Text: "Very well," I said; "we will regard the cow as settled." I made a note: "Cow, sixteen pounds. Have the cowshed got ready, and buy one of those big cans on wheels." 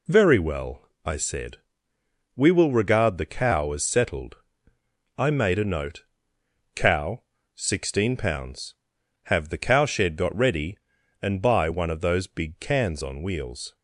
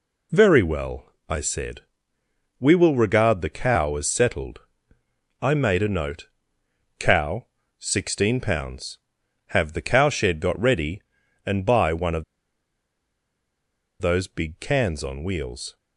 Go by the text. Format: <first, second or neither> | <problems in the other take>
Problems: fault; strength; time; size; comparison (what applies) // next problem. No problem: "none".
first | pauses between "of" and "those"; strong; at 12.2 s; 1.7 s long